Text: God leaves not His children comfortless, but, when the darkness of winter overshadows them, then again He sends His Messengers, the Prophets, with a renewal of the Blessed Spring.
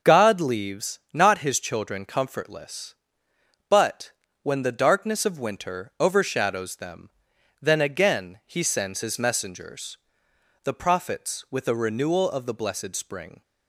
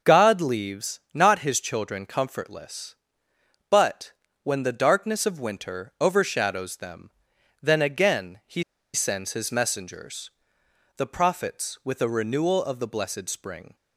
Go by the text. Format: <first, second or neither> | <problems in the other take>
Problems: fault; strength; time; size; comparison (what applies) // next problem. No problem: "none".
first | starts louder than the rest; noticeable; until 1.2 s; 6 dB; noticeable in the first // pauses between "leaves" and "not"; slight; at 0.9 s; 0.16 s long; slight in the first // pauses between "He" and "sends"; slight; at 8.6 s; 0.31 s long